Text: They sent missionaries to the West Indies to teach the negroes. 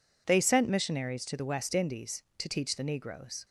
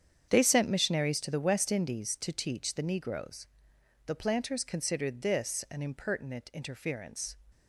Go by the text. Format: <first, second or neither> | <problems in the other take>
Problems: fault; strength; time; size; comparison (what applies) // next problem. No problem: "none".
first | starts louder than the rest; strong; until 1.2 s; 8 dB // goes on to say "The planters considered this an impertinent interference"; strong; from 4.0 s on; 3.3 s long